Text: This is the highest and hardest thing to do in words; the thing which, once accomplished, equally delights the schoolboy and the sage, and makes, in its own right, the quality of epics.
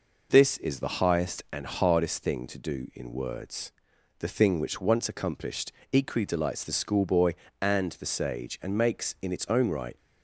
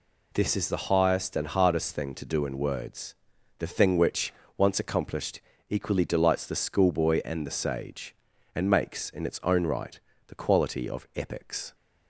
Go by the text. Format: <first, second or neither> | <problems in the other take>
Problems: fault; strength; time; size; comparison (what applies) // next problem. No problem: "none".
second | stops before "the quality of epics"; at 9.9 s